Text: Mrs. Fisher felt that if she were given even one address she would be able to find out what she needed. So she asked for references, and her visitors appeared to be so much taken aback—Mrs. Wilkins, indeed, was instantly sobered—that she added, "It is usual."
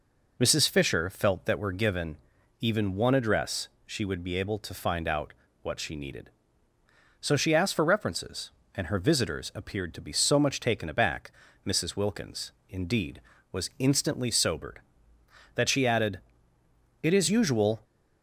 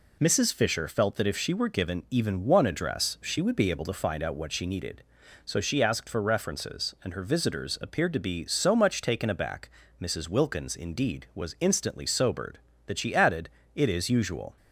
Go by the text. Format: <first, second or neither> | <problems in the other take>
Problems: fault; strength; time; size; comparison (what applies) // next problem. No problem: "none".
second | skips "if she"; at 1.5 s // pauses between "given" and "even"; at 2.1 s; 0.42 s long // pauses between "address" and "she"; slight; at 3.6 s; 0.18 s long // pauses between "out" and "what"; slight; at 5.3 s; 0.28 s long